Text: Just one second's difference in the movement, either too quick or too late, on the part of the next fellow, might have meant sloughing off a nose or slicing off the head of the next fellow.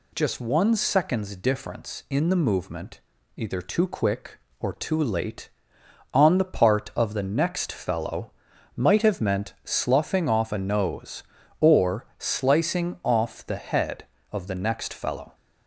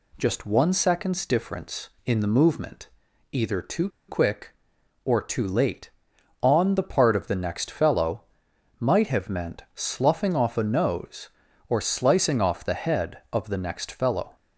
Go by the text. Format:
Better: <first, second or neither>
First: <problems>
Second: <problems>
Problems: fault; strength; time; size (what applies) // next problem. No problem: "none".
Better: first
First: none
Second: pauses between "too" and "quick"; slight; at 3.8 s; 0.20 s long